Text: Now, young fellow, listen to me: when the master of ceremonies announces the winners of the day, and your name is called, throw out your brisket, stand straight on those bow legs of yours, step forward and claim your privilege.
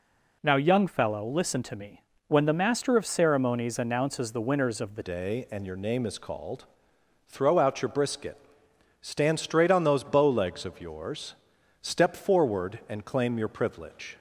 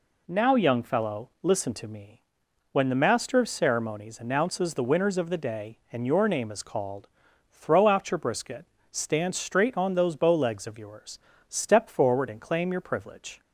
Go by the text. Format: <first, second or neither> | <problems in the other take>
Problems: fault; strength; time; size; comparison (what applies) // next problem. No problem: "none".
second | changes voice at "day"; from 5.0 s on; 9.1 s long